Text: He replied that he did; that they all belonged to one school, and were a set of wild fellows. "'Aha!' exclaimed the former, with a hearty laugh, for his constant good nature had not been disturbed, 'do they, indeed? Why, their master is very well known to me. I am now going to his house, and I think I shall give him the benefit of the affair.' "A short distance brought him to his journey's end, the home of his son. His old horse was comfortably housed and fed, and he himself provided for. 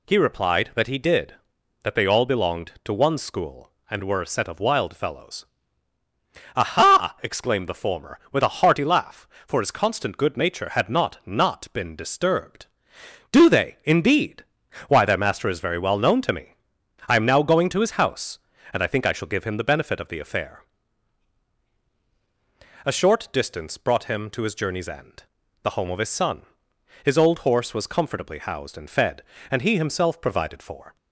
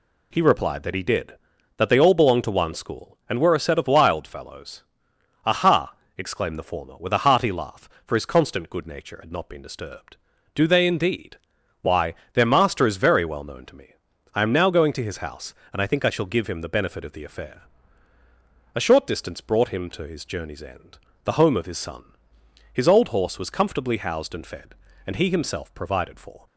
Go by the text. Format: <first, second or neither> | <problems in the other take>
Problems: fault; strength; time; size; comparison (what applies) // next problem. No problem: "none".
second | says "not" twice; at 11.2 s